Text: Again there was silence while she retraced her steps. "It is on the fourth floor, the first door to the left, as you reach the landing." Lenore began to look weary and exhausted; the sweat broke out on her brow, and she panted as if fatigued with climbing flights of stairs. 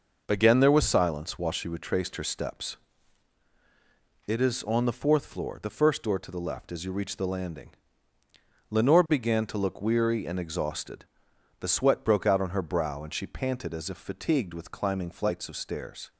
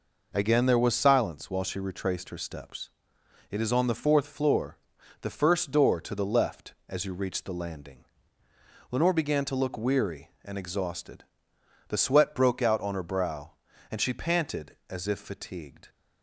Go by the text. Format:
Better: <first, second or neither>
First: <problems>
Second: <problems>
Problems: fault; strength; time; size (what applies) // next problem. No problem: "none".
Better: first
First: none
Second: stops before "with climbing flights of stairs"; at 15.8 s